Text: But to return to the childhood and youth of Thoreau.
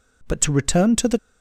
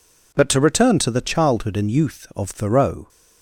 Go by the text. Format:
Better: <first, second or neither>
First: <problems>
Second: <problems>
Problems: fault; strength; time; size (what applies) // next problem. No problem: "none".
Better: second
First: stops before "childhood and youth of Thoreau"; at 1.1 s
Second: none